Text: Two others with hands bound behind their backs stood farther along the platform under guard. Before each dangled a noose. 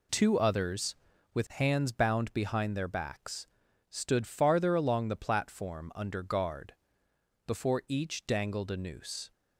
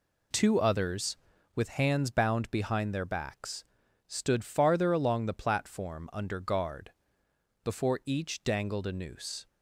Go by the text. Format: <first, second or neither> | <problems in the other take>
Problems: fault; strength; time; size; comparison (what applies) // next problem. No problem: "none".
neither | pauses between "backs" and "stood"; the same in both